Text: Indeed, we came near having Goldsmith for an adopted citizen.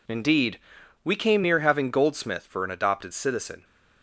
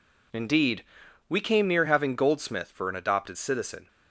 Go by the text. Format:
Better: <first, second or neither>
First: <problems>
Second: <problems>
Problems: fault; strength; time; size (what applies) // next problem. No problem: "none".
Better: neither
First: none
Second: none